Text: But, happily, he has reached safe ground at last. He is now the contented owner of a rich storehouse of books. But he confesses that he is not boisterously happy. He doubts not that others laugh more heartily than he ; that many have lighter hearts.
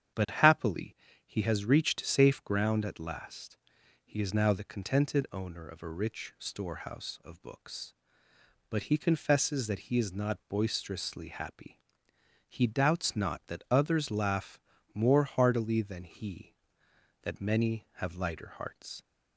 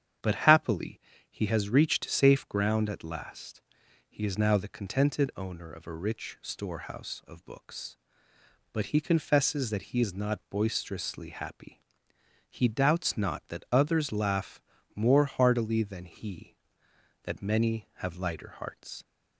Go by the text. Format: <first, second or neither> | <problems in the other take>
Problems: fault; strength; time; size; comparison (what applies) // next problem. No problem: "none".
neither | starts louder than the rest; strong; the same in both // pauses between "laugh" and "more"; slight; the same in both